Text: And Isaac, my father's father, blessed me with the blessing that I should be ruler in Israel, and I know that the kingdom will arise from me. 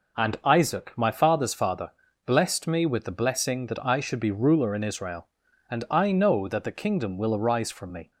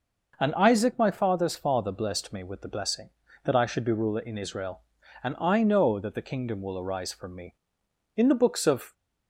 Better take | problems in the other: first | goes on to say "In the books of"; noticeable; from 8.1 s on; 0.78 s long

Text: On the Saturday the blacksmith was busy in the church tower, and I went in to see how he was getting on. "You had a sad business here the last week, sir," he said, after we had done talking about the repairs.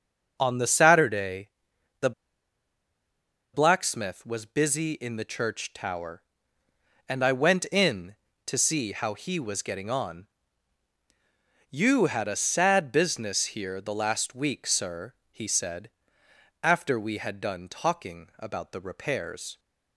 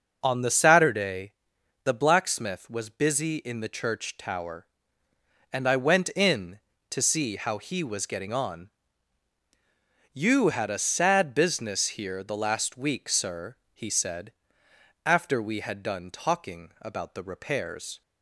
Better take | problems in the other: second | starts louder than the rest; noticeable; until 1.4 s; 6 dB; noticeable in the second // pauses between "Saturday" and "the"; noticeable; at 1.4 s; 0.52 s long; noticeable in the second // pauses between "the" and "blacksmith"; strong; at 2.1 s; 1.4 s long

